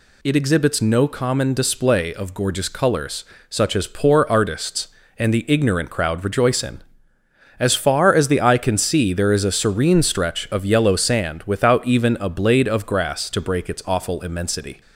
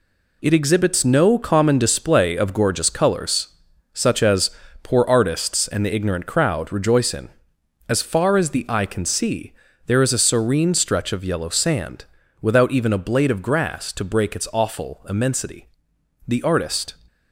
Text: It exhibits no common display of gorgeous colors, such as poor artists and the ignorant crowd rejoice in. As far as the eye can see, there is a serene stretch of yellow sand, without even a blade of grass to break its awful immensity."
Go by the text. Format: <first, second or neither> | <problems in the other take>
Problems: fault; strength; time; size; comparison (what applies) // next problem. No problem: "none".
first | pauses between "as" and "poor"; slight; at 4.4 s; 0.34 s long // goes on to say "The artist"; noticeable; from 16.2 s on; 0.68 s long